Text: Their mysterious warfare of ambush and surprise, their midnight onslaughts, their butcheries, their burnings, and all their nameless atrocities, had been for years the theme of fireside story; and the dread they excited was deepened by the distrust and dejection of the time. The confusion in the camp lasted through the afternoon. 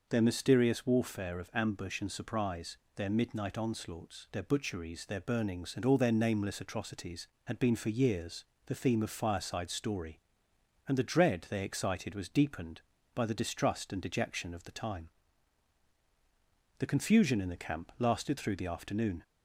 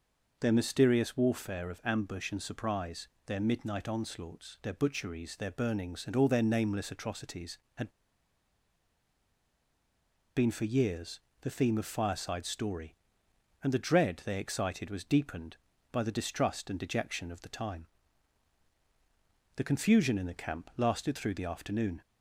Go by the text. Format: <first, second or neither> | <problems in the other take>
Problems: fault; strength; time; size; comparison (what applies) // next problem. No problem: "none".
first | pauses between "had" and "been"; strong; at 7.9 s; 2.4 s long // pauses between "years" and "the"; slight; at 11.1 s; 0.22 s long; slight in the first